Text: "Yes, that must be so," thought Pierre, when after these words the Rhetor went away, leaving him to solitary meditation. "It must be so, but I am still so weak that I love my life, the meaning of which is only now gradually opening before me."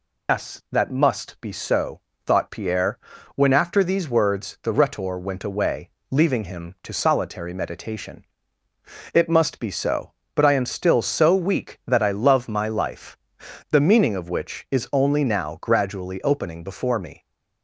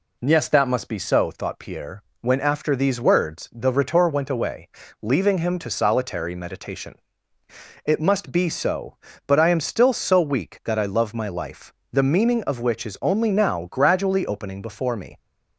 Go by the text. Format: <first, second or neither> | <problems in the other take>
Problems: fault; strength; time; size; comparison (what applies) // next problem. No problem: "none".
second | loses the start of "Yes"; at 0.2 s; 120 ms